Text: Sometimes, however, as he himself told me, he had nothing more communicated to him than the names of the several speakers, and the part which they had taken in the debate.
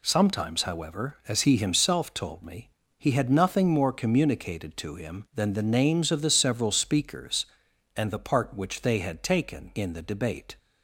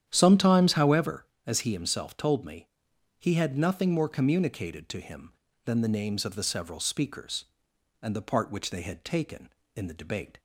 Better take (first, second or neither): first